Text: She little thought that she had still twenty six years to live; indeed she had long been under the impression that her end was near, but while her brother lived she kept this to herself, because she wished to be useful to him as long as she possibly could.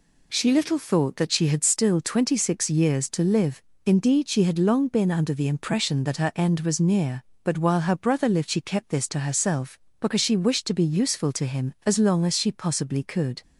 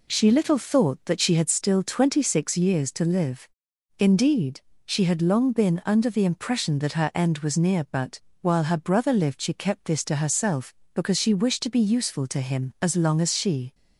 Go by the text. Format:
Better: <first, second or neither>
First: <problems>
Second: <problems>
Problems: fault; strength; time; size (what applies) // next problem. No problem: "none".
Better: first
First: none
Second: pauses between "indeed" and "she"; slight; at 4.6 s; 0.26 s long // pauses between "but" and "while"; slight; at 8.1 s; 0.22 s long // stops before "possibly could"; at 13.7 s